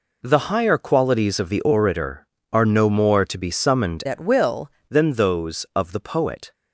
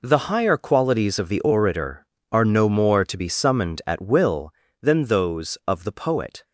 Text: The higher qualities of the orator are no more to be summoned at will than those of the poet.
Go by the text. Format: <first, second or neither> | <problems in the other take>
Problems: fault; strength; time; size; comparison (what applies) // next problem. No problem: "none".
second | changes voice from "at" to "will"; from 4.0 to 4.6 s; 0.6 s long